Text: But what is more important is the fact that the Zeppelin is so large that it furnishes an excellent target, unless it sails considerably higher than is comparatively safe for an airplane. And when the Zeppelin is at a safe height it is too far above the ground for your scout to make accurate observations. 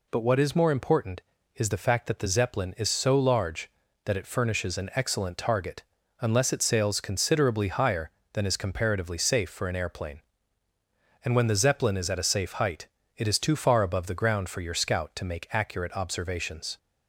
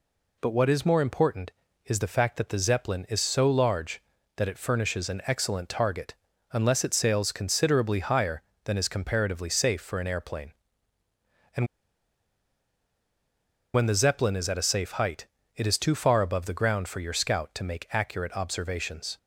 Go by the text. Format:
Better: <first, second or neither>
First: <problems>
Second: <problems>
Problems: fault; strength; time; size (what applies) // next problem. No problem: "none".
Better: first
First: pauses between "height" and "it"; slight; at 12.8 s; 0.30 s long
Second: pauses between "And" and "when"; strong; at 11.6 s; 2.0 s long // pauses between "height" and "it"; slight; at 15.2 s; 0.30 s long